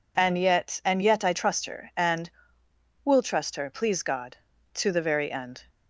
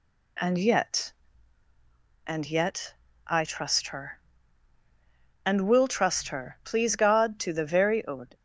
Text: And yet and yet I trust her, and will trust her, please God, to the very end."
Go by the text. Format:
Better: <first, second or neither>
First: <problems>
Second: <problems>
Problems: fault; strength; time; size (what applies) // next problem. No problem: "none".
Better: first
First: none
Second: pauses between "yet" and "I"; slight; at 2.9 s; 0.32 s long // stops before "end"; at 8.3 s